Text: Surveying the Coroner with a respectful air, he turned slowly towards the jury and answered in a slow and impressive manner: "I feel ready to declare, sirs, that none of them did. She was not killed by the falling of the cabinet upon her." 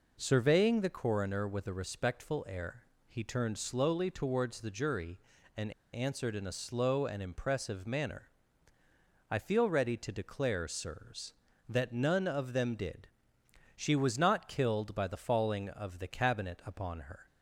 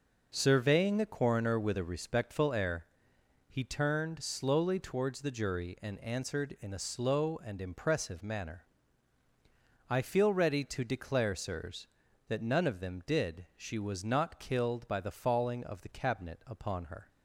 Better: second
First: pauses between "and" and "answered"; slight; at 5.7 s; 0.22 s long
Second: none

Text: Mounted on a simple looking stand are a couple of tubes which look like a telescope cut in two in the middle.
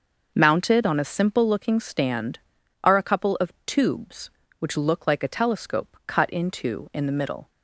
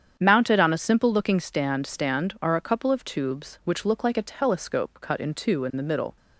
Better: first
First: starts louder than the rest; noticeable; until 1.3 s; 6 dB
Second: starts louder than the rest; strong; until 1.2 s; 8.5 dB // says "stand" twice; at 1.8 s

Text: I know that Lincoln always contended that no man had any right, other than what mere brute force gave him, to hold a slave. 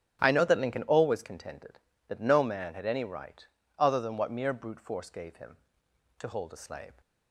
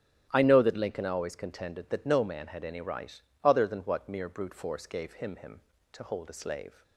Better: first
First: starts louder than the rest; strong; until 1.2 s; 8 dB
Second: starts louder than the rest; strong; until 1.3 s; 10.5 dB // says "him" twice; at 5.3 s

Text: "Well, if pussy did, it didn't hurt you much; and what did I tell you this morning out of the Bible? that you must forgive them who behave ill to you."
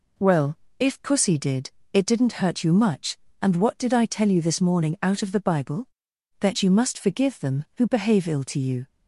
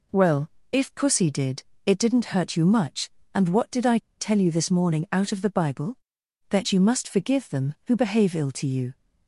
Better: first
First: none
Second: pauses between "I" and "tell"; slight; at 3.9 s; 0.19 s long

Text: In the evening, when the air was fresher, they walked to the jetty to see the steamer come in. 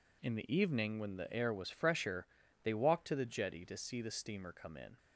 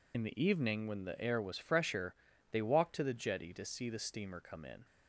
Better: first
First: none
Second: loses the start of "In"; at 0.1 s; 60 ms

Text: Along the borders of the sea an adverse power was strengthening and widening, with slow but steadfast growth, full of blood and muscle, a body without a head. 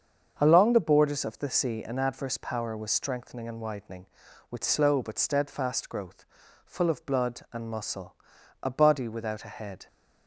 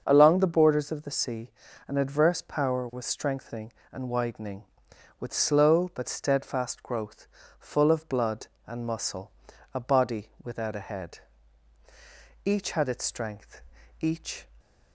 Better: first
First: starts louder than the rest; until 1.4 s; 7 dB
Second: starts louder than the rest; until 1.0 s; 6.5 dB // pauses between "sea" and "an"; slight; at 1.4 s; 0.36 s long // goes on to say "Each had its strength each"; strong; from 12.4 s on; 2.0 s long

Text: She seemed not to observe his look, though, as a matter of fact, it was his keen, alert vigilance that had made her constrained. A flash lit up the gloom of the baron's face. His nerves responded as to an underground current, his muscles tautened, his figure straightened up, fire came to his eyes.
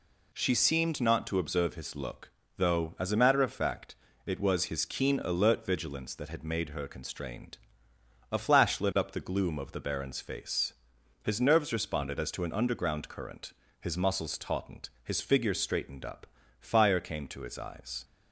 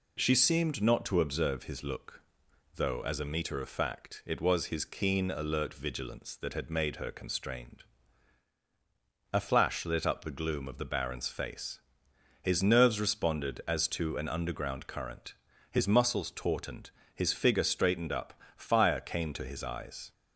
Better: first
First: none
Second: says "meter" for "matter"; at 3.2 s

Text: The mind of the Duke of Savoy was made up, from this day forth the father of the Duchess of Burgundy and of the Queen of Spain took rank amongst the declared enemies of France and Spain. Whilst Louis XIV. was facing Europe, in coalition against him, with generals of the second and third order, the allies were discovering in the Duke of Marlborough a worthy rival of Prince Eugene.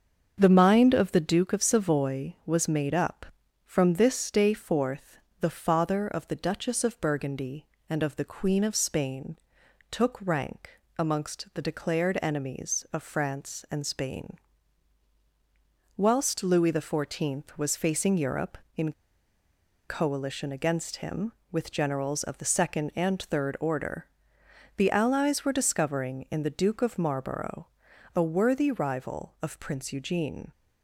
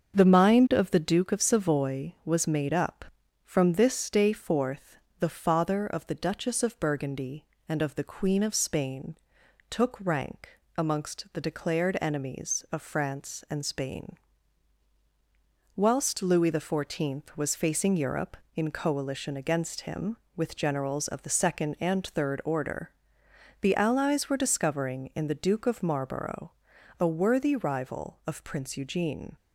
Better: second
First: starts louder than the rest; until 1.3 s; 7 dB // pauses between "forth" and "the"; slight; at 5.1 s; 0.24 s long // pauses between "Spain" and "took"; noticeable; at 9.3 s; 0.54 s long // pauses between "rank" and "amongst"; slight; at 10.7 s; 0.18 s long // pauses between "in" and "coalition"; noticeable; at 18.9 s; 0.95 s long // pauses between "Marlborough" and "a"; noticeable; at 27.6 s; 0.48 s long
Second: starts louder than the rest; until 1.1 s; 7 dB // pauses between "forth" and "the"; slight; at 4.9 s; 0.24 s long // pauses between "Spain" and "took"; noticeable; at 9.1 s; 0.54 s long // pauses between "rank" and "amongst"; slight; at 10.5 s; 0.18 s long // pauses between "Marlborough" and "a"; noticeable; at 26.4 s; 0.48 s long

